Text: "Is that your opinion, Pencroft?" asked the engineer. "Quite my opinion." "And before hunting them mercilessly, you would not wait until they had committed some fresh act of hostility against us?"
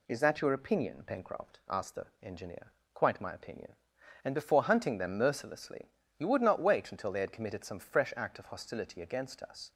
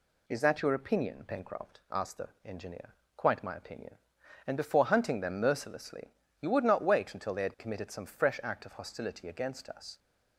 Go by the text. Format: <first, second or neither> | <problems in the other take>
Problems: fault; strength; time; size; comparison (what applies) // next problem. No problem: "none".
neither | none